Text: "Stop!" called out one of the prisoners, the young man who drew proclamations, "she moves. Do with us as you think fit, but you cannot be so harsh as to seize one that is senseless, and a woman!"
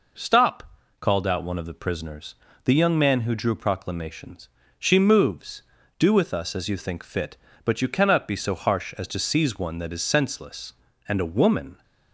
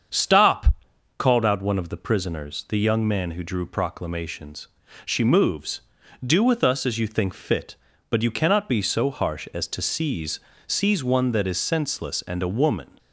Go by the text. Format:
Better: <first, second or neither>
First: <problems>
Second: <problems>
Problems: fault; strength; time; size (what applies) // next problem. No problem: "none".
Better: first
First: none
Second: starts louder than the rest; until 1.5 s; 7 dB // says "seize" twice; at 10.6 s